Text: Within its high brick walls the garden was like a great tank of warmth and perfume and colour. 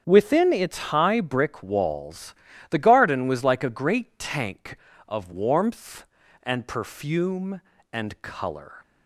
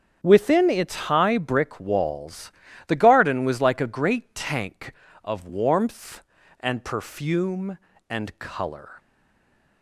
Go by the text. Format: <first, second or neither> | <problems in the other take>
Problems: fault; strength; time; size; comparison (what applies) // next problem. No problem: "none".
first | starts louder than the rest; strong; until 1.4 s; 9 dB; strong in the first // pauses between "its" and "high"; slight; at 0.9 s; 0.16 s long; slight in the first // pauses between "walls" and "the"; slight; at 2.5 s; 0.34 s long; slight in the first // stays silent after the last word; slight; from 8.9 s on; 0.9 s long